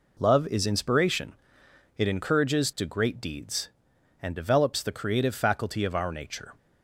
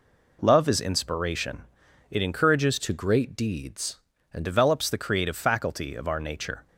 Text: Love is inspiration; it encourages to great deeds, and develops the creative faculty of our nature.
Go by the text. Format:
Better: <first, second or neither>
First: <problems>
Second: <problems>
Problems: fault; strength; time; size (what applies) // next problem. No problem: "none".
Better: first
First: none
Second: changes voice from "to" to "and"; from 2.7 to 4.4 s; 1.7 s long